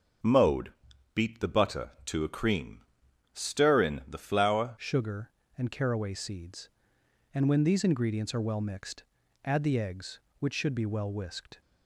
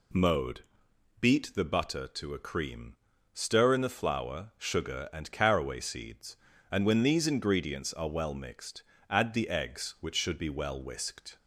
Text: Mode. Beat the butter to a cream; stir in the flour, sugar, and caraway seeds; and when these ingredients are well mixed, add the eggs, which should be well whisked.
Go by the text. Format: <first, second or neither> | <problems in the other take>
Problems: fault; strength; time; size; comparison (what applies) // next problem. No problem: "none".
second | starts louder than the rest; until 1.6 s; 6.5 dB // changes voice at "sugar"; from 4.7 s on; 6.9 s long